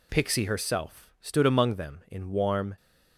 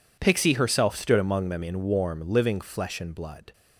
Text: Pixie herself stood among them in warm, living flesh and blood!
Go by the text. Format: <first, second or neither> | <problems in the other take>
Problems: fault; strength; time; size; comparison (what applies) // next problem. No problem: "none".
second | stops before "living flesh and blood"; at 2.7 s